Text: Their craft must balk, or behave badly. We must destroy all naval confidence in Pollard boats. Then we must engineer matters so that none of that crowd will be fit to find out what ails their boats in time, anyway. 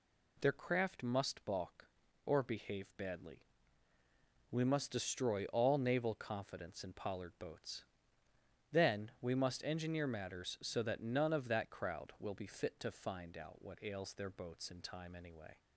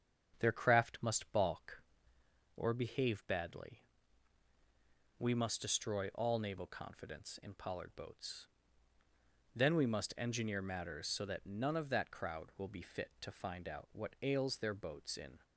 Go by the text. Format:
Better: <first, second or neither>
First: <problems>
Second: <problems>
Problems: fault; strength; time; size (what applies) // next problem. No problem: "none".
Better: first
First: none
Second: starts louder than the rest; strong; until 1.4 s; 8 dB // stops before "time anyway"; at 15.4 s